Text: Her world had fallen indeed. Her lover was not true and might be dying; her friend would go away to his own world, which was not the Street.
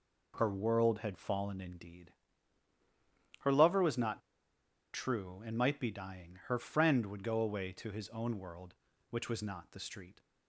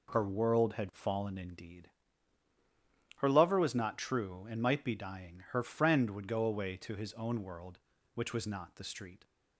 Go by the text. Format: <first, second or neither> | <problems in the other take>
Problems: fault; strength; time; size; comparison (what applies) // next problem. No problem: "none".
second | pauses between "not" and "true"; noticeable; at 4.1 s; 0.74 s long